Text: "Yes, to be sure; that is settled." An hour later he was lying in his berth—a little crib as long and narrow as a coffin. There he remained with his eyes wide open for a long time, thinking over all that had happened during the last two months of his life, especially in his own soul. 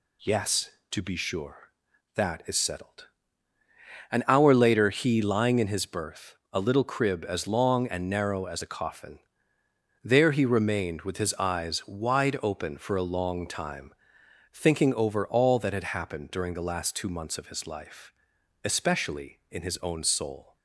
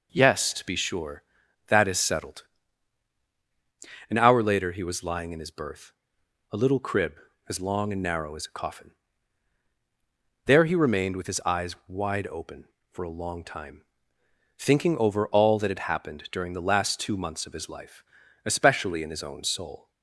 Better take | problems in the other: second | skips "was"; at 5.2 s

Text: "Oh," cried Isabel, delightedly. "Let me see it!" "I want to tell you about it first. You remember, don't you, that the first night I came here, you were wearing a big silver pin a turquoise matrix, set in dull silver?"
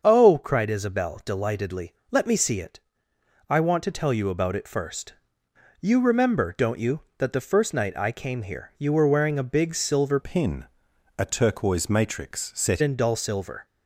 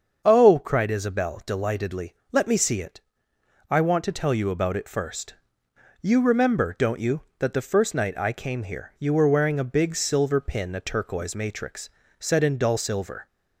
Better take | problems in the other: second | starts louder than the rest; until 1.0 s; 7 dB; also in the second // changes voice from "pin" to "set"; from 10.2 to 12.8 s; 2.6 s long // pauses between "pin" and "a"; noticeable; at 10.6 s; 0.54 s long

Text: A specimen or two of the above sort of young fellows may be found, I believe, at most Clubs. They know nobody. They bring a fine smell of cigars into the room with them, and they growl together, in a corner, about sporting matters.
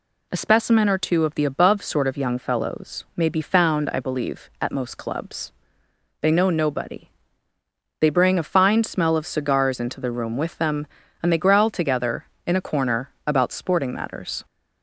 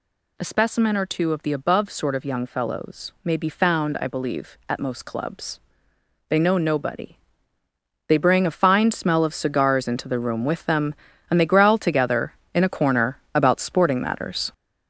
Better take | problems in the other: first | gets louder; throughout; 6.5 dB

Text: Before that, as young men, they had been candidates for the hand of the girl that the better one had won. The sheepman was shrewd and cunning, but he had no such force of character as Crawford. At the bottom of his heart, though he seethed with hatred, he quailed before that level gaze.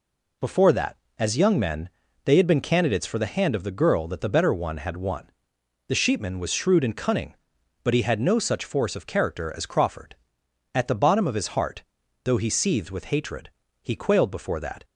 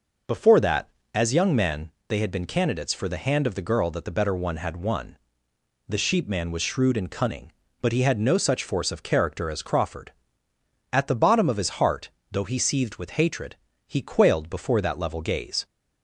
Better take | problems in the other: second | stops before "level gaze"; at 14.8 s

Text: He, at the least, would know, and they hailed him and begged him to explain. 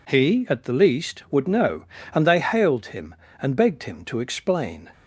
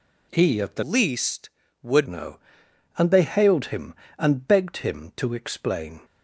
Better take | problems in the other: first | changes voice from "least" to "would"; from 0.8 to 2.0 s; 1.2 s long

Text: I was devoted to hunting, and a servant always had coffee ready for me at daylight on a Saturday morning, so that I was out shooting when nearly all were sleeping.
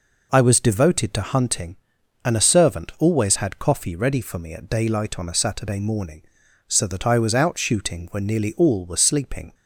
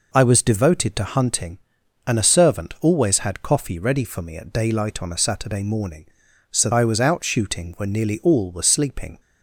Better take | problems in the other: first | skips "that"; at 6.7 s

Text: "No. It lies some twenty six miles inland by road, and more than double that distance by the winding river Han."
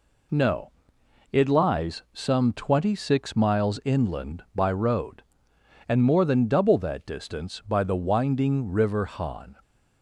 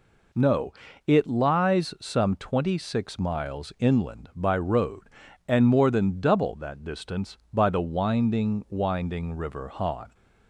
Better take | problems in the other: first | says "winding" twice; at 8.6 s

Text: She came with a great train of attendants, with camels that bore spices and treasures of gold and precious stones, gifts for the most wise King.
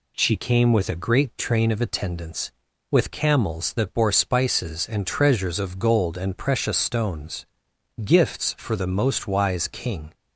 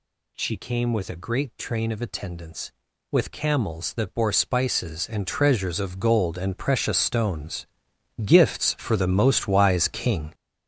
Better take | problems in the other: first | gets louder; strong; throughout; 9 dB

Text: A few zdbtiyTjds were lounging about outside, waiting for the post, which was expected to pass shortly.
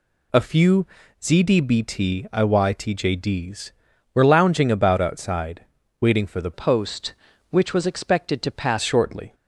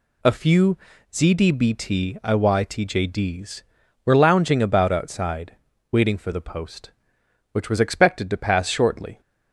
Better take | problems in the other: second | pauses between "few" and "zdbtiyTjds"; slight; at 0.8 s; 0.34 s long; slight in the second // changes voice from "post" to "pass"; from 6.5 to 8.7 s; 2.2 s long

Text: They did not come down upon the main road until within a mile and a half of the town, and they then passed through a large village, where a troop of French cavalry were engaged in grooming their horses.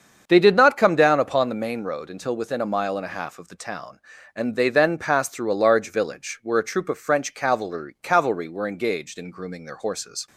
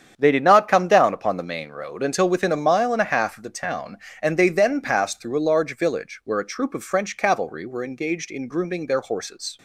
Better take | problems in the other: second | starts louder than the rest; strong; until 1.2 s; 7 dB; strong in the second // says "cavalry" twice; at 8.0 s

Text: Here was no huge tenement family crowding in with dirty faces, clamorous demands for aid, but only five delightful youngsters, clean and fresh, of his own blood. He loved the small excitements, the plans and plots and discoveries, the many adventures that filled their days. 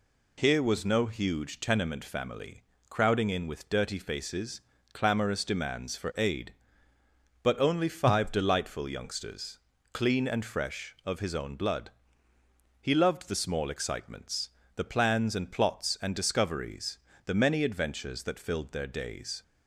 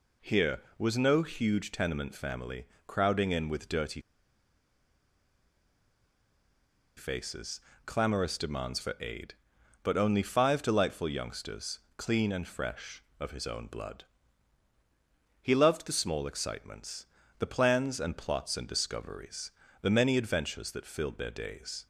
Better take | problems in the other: first | pauses between "family" and "crowding"; slight; at 2.6 s; 0.22 s long; slight in the first // pauses between "dirty" and "faces"; strong; at 4.0 s; 2.9 s long

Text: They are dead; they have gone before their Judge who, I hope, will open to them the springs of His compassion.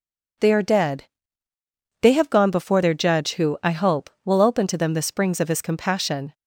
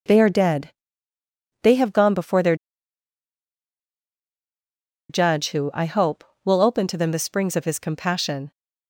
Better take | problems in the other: first | pauses between "their" and "Judge"; strong; at 2.5 s; 2.5 s long

